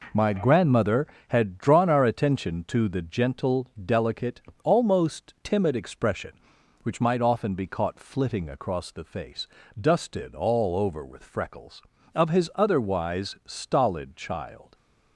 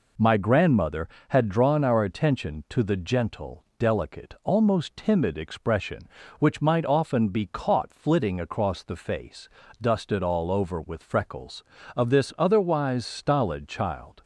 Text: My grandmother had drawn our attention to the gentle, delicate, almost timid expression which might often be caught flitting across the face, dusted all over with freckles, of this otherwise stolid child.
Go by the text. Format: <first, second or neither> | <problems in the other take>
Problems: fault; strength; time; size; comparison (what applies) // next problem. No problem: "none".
second | says "his" for "this"; at 12.2 s